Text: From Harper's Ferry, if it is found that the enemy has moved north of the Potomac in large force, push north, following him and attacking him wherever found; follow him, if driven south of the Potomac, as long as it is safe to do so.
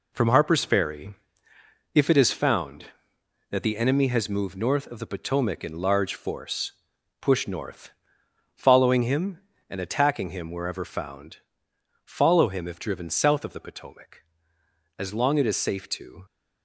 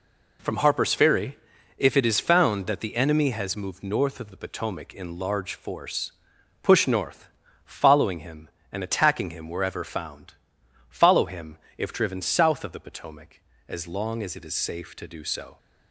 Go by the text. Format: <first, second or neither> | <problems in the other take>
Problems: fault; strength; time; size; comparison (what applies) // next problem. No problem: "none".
second | stops before "do so"; at 16.2 s